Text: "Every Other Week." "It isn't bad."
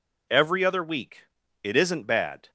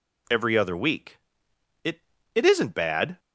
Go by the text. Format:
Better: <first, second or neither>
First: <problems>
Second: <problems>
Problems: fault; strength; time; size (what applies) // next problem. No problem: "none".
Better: first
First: none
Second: says "It" twice; at 2.3 s